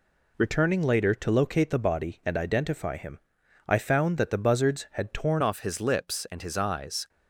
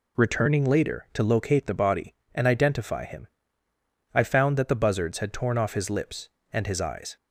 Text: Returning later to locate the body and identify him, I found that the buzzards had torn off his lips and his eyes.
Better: second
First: changes voice at "off"; from 5.4 s on; 1.6 s long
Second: none

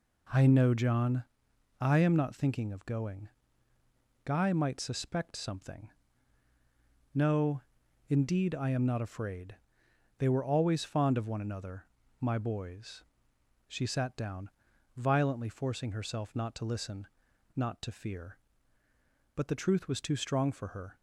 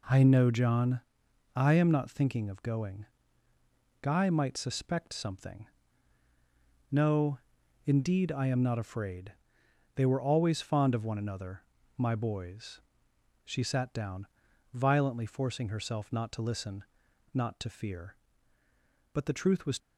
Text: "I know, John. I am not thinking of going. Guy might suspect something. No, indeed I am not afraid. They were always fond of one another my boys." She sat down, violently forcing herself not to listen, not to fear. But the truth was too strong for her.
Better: first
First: pauses between "another" and "my"; slight; at 11.8 s; 0.34 s long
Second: pauses between "another" and "my"; slight; at 11.6 s; 0.34 s long // stops before "too strong for her"; at 19.7 s

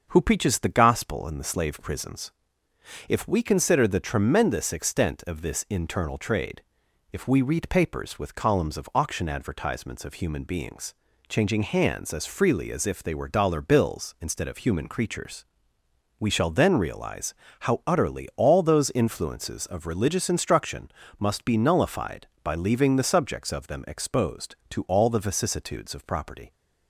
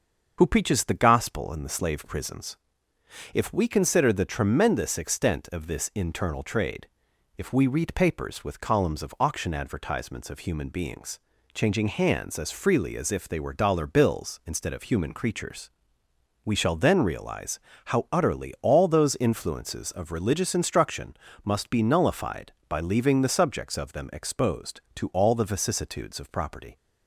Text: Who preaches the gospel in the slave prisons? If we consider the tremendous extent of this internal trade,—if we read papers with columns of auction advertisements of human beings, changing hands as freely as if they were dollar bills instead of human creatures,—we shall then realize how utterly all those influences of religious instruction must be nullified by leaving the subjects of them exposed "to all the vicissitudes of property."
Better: first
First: starts louder than the rest; until 1.1 s; 6.5 dB // pauses between "realize" and "how"; slight; at 17.3 s; 0.26 s long // pauses between "instruction" and "must"; slight; at 20.8 s; 0.30 s long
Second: loses the start of "Who"; at 0.3 s; 40 ms // starts louder than the rest; until 1.3 s; 6.5 dB // pauses between "realize" and "how"; slight; at 17.6 s; 0.26 s long // pauses between "instruction" and "must"; slight; at 21.1 s; 0.30 s long

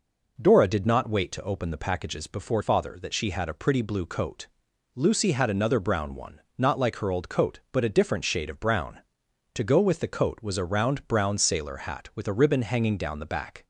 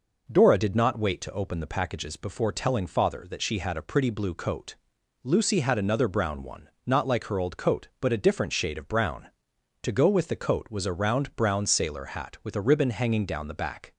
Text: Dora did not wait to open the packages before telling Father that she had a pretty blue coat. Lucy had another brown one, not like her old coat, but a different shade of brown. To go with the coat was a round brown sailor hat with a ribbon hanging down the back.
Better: second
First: skips "telling"; at 2.6 s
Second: none

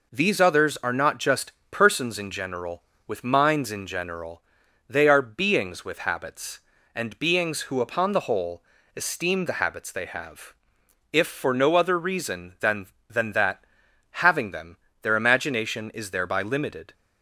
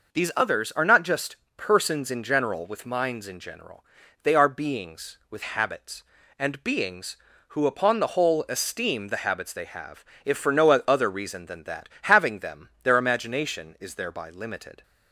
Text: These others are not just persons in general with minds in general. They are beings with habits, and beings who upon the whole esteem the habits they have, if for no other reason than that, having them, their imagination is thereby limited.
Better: second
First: pauses between "just" and "persons"; slight; at 1.5 s; 0.20 s long // pauses between "whole" and "esteem"; slight; at 8.6 s; 0.32 s long // says "than" twice; at 13.0 s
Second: pauses between "just" and "persons"; slight; at 1.3 s; 0.20 s long

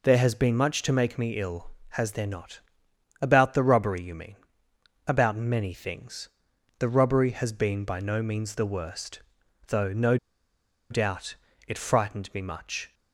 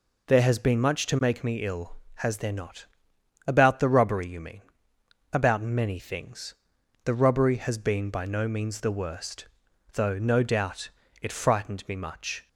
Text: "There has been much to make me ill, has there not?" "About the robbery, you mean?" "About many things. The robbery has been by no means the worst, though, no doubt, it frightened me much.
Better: second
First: pauses between "no" and "doubt"; noticeable; at 10.1 s; 0.74 s long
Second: none

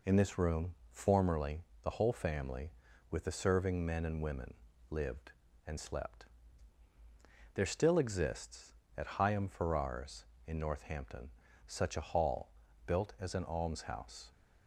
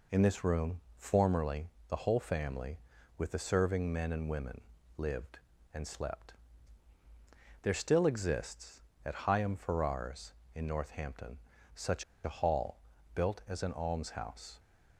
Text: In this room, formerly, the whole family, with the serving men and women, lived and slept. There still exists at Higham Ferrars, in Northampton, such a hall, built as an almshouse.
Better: first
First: none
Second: pauses between "such" and "a"; slight; at 12.0 s; 0.21 s long

